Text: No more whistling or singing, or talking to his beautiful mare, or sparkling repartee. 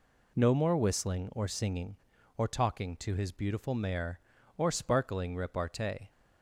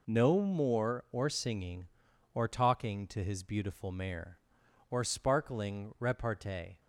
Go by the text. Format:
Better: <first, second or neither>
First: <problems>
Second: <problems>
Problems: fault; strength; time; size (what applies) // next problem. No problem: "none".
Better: first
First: none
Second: skips "whistling"; at 1.0 s